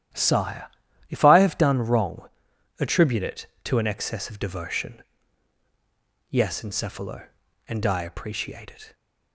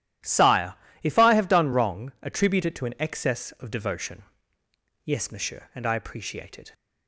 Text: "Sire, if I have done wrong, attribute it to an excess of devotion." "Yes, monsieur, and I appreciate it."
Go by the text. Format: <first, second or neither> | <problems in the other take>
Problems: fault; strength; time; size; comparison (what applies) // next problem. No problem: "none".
second | starts louder than the rest; strong; until 1.5 s; 11.5 dB; strong in the second // says "encephalo" for "monsieur"; at 6.6 s